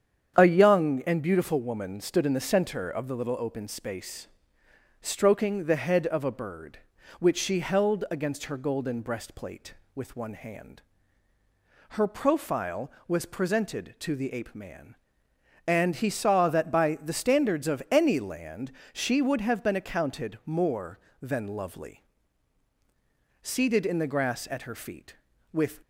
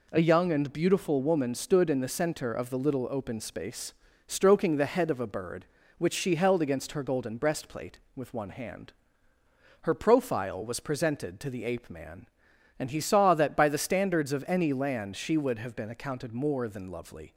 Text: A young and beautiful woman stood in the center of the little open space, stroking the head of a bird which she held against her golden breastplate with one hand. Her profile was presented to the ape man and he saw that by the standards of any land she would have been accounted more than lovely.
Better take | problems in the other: second | starts louder than the rest; strong; until 1.4 s; 8.5 dB // pauses between "land" and "she"; slight; at 18.7 s; 0.20 s long // goes on to say "Seated in the grass at her feet with"; strong; from 23.4 s on; 2.3 s long

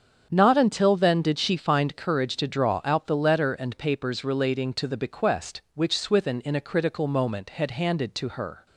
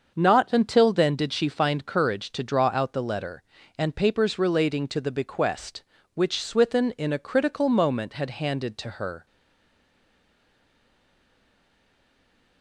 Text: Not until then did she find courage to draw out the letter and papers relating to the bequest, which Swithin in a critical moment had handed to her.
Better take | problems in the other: first | starts louder than the rest; until 1.1 s; 6.5 dB; strong in the first // stays silent after the last word; strong; from 9.2 s on; 3.4 s long

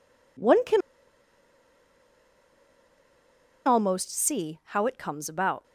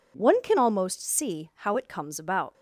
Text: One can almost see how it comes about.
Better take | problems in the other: second | pauses between "can" and "almost"; strong; at 0.8 s; 2.8 s long

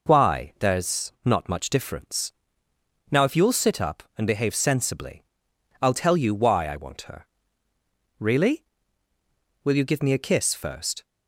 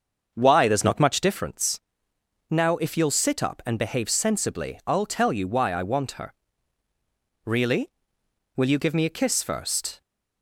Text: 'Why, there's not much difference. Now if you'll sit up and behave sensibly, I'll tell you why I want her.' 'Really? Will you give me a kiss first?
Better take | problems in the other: first | starts louder than the rest; until 1.4 s; 6.5 dB

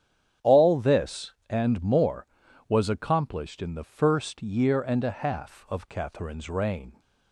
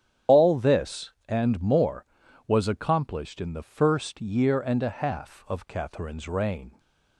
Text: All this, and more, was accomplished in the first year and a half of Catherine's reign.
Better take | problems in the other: first | loses the start of "All"; at 0.2 s; 85 ms // starts louder than the rest; strong; until 1.4 s; 9.5 dB; strong in the first

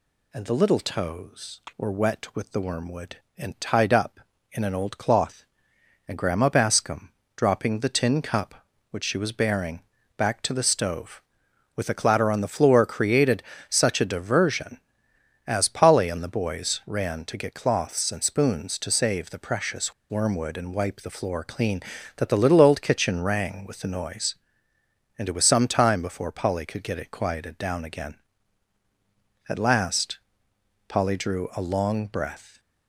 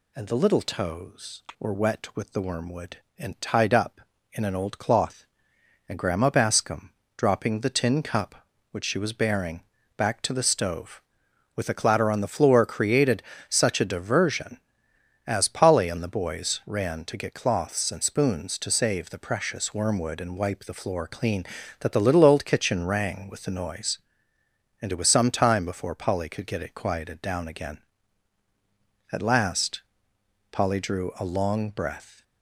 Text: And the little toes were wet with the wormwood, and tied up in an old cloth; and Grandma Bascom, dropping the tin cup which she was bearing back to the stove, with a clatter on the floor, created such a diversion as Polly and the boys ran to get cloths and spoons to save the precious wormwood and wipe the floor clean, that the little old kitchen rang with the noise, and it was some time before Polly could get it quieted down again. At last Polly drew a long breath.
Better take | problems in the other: second | pauses between "bearing" and "back"; slight; at 9.8 s; 0.36 s long; slight in the second // pauses between "created" and "such"; slight; at 13.4 s; 0.28 s long; slight in the second // pauses between "precious" and "wormwood"; slight; at 19.9 s; 0.18 s long // pauses between "last" and "Polly"; noticeable; at 30.1 s; 0.68 s long; noticeable in the second

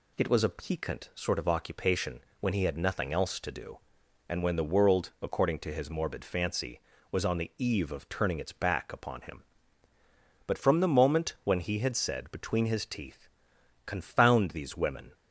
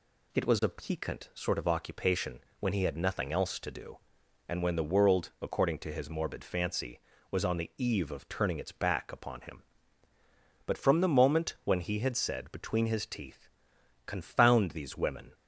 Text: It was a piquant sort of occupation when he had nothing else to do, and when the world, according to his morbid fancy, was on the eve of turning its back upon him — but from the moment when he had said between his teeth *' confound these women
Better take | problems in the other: neither | pauses between "occupation" and "when"; slight; the same in both

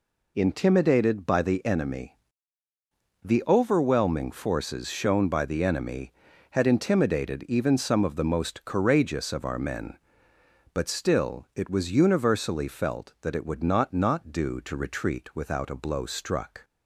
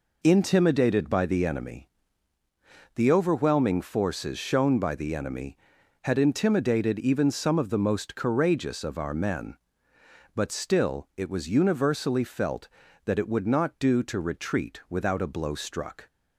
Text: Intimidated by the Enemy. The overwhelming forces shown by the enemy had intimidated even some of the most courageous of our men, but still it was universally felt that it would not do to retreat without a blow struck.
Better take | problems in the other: second | says "not" twice; at 13.9 s

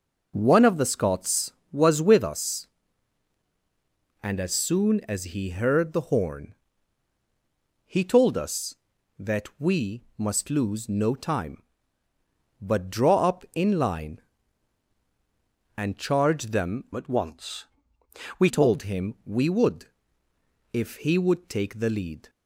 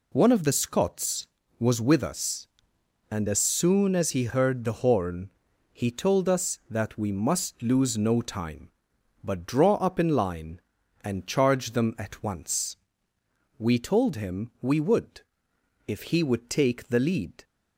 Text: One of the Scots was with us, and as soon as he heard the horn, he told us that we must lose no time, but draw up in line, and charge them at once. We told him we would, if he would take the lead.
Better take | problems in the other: second | pauses between "we" and "must"; slight; at 10.0 s; 0.16 s long // changes voice from "at" to "We"; from 16.9 to 18.4 s; 1.5 s long

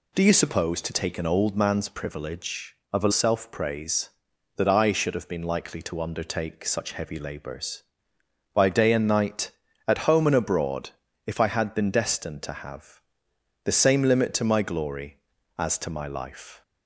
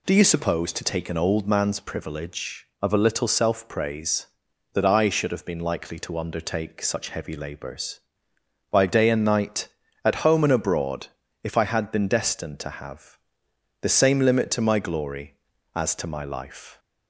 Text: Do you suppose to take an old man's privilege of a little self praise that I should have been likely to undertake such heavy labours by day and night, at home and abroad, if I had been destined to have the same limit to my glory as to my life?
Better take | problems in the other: second | skips "little"; at 3.1 s // pauses between "have" and "the"; noticeable; at 12.9 s; 0.62 s long; noticeable in the second

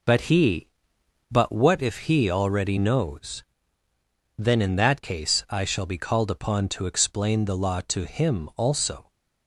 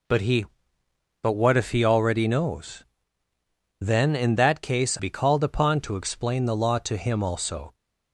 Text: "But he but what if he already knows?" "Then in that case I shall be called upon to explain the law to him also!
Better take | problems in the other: first | skips "I shall"; at 4.9 s

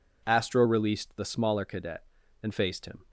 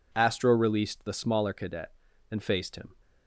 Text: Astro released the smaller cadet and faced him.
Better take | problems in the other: neither | none

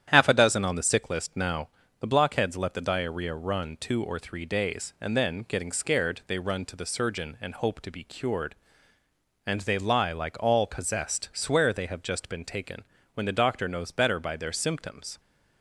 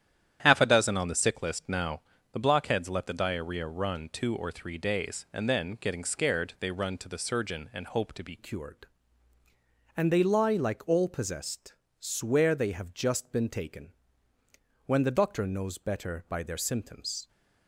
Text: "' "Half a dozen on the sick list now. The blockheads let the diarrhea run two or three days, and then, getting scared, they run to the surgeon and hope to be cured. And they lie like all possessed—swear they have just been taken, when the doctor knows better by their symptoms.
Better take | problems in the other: first | starts louder than the rest; strong; until 1.4 s; 10.5 dB; strong in the first // changes voice at "cured"; from 8.3 s on; 8.9 s long

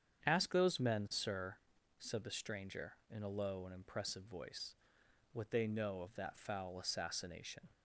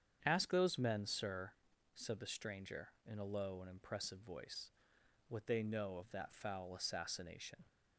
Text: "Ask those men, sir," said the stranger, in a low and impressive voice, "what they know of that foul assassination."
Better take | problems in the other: neither | starts louder than the rest; strong; the same in both

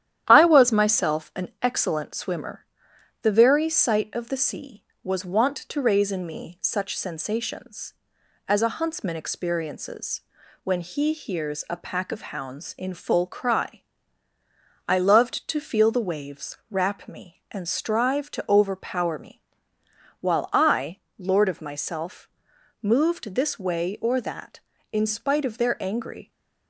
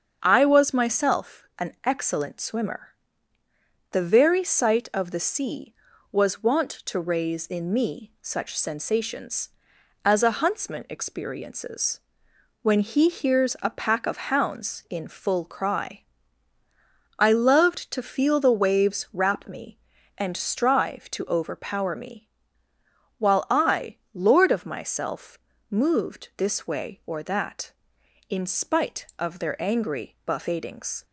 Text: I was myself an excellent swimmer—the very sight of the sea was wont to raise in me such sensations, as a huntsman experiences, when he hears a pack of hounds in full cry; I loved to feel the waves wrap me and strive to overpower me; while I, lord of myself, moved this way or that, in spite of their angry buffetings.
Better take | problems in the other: second | starts louder than the rest; strong; until 1.2 s; 11 dB; also in the second // stops before "buffetings"; at 26.3 s

